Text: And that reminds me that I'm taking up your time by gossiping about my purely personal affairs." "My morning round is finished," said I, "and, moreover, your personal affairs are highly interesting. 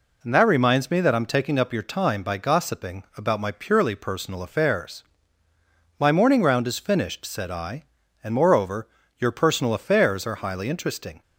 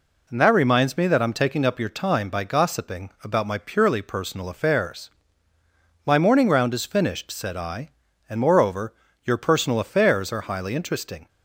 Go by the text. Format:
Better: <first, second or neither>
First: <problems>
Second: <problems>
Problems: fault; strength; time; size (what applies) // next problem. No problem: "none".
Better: neither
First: none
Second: none